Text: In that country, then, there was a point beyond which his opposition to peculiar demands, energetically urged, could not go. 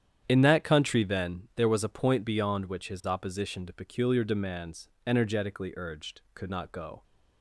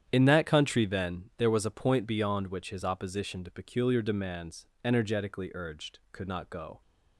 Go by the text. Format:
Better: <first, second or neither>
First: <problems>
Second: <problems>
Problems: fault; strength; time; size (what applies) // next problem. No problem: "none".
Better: neither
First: starts louder than the rest; strong; until 1.2 s; 9.5 dB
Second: starts louder than the rest; strong; until 1.0 s; 9.5 dB